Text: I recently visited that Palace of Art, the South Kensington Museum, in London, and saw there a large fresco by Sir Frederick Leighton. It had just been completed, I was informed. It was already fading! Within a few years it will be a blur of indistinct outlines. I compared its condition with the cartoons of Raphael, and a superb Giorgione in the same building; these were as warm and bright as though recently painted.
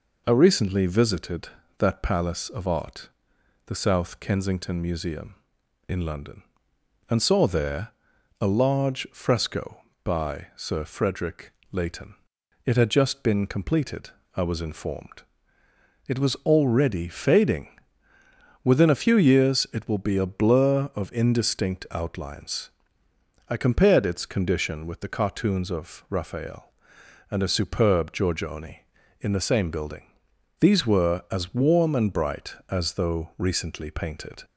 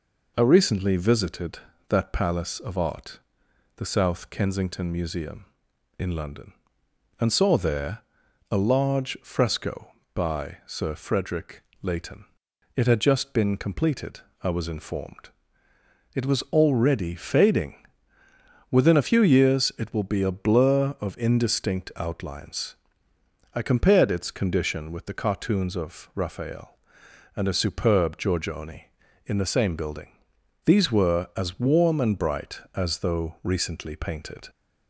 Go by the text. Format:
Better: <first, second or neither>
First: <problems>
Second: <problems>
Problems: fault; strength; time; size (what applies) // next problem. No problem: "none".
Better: neither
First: pauses between "there" and "a"; noticeable; at 7.8 s; 0.50 s long // pauses between "Frederick" and "Leighton"; slight; at 11.5 s; 0.20 s long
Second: pauses between "there" and "a"; noticeable; at 8.0 s; 0.50 s long // pauses between "Frederick" and "Leighton"; slight; at 11.6 s; 0.20 s long